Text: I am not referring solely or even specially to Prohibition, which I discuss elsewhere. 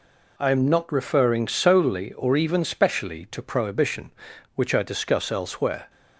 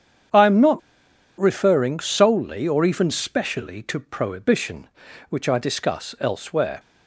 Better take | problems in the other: first | starts louder than the rest; strong; until 1.9 s; 8.5 dB // pauses between "not" and "referring"; noticeable; at 0.7 s; 0.58 s long

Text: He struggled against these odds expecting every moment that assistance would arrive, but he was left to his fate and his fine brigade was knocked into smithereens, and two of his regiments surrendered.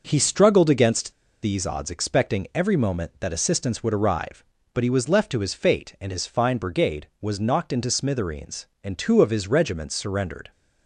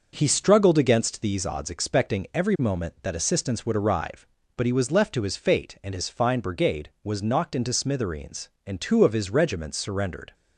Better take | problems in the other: second | pauses between "against" and "these"; slight; at 1.1 s; 0.29 s long

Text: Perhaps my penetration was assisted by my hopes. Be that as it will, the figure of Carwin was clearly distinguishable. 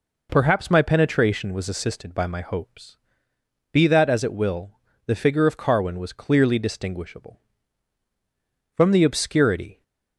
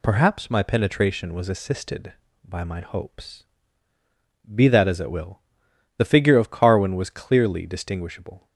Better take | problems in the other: second | goes on to say "From the obscurity"; noticeable; from 8.7 s on; 1.0 s long

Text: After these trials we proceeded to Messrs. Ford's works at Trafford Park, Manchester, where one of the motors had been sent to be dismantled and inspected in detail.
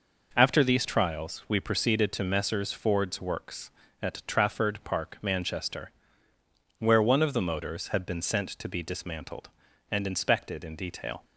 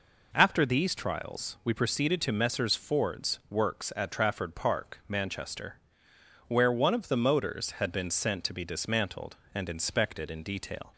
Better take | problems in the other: neither | none

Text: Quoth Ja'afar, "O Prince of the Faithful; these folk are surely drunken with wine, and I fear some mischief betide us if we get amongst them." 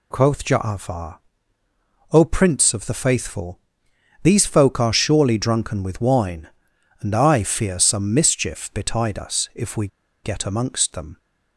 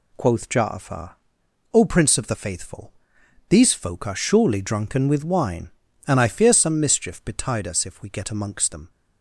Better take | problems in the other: second | pauses between "we" and "get"; at 9.8 s; 0.36 s long

